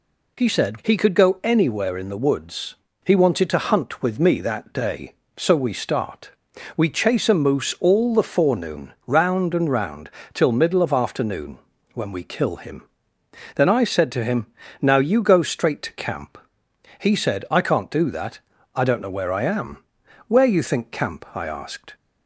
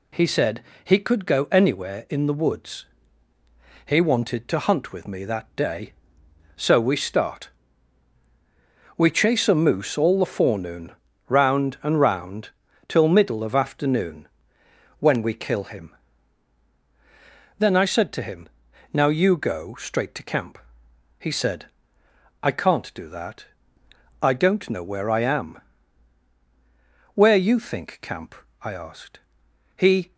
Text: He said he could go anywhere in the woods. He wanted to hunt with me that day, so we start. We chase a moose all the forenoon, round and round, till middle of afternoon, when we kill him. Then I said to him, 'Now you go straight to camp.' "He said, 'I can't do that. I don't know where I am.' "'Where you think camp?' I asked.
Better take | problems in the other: first | pauses between "said" and "he"; slight; at 0.6 s; 0.22 s long // goes on to say "He"; slight; from 29.7 s on; 0.38 s long

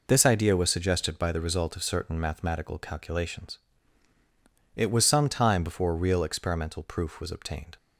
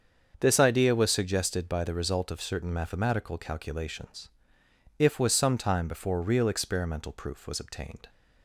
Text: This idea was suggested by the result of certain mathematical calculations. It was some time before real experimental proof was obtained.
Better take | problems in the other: first | starts louder than the rest; until 1.4 s; 7 dB // says "If" for "It"; at 4.9 s

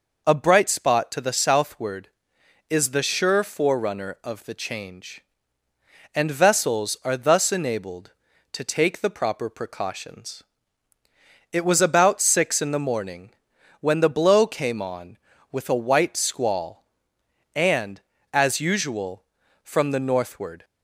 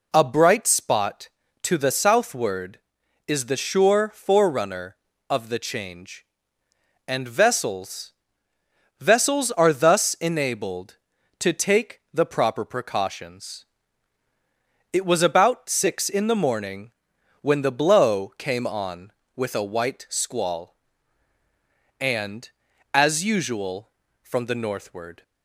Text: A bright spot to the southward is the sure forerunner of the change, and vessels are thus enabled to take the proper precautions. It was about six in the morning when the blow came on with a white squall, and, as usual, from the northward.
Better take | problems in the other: first | says "vessels" twice; at 9.0 s // pauses between "morning" and "when"; noticeable; at 16.9 s; 0.50 s long; noticeable in the first

